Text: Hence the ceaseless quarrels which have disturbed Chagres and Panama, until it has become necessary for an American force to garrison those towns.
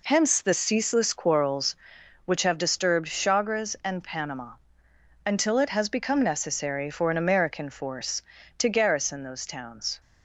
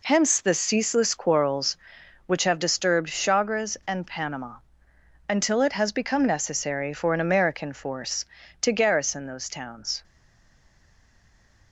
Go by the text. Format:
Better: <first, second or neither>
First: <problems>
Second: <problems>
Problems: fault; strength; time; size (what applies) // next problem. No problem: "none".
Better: first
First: none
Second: stays silent after the last word; noticeable; from 10.0 s on; 1.7 s long